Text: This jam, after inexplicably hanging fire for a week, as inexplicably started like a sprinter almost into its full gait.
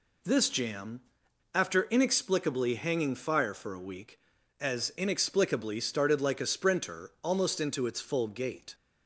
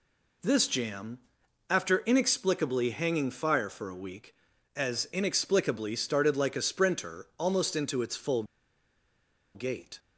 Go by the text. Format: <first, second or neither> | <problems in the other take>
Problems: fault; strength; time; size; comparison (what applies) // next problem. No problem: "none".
first | pauses between "full" and "gait"; at 8.4 s; 1.1 s long